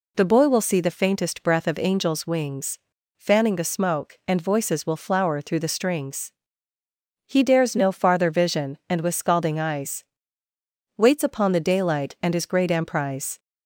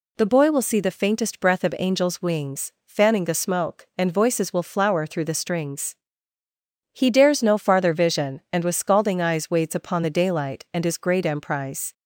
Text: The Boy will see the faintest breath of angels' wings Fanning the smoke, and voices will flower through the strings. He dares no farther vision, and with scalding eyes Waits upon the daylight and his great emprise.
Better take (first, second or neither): second